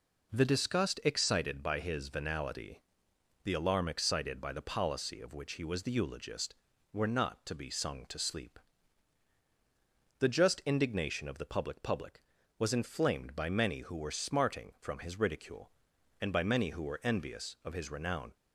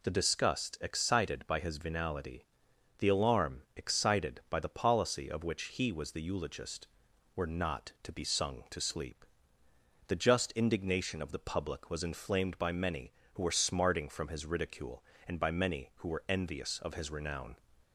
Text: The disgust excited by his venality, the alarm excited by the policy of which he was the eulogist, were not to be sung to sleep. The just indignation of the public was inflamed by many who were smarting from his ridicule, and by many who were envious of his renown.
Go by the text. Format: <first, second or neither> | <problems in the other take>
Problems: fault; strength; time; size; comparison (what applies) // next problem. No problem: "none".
second | says "public" twice; at 11.8 s